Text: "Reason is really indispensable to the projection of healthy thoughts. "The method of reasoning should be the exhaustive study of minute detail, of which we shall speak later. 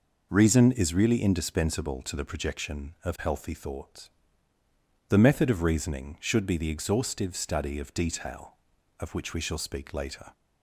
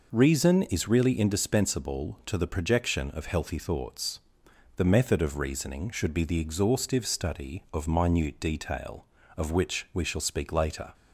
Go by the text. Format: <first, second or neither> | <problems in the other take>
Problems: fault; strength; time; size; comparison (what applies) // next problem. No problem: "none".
second | skips "minute"; at 7.9 s